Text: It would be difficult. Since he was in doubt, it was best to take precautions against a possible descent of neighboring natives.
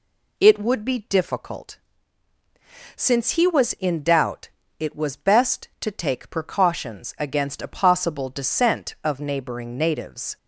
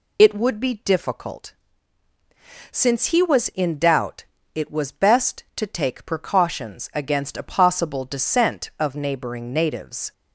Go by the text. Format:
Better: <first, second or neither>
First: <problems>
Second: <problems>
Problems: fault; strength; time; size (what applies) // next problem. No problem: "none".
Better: first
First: none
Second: loses the start of "It"; at 0.1 s; 55 ms